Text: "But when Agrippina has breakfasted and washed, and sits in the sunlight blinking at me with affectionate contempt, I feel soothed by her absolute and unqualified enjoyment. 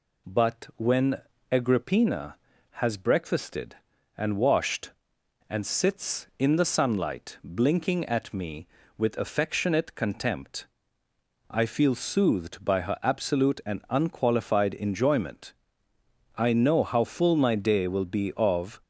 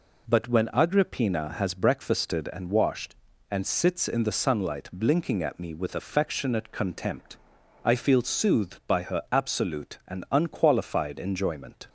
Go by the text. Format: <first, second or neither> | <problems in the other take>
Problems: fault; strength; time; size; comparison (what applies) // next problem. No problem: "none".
second | pauses between "when" and "Agrippina"; slight; at 1.2 s; 0.28 s long // goes on to say "I know how full my day will be of"; strong; from 16.3 s on; 2.4 s long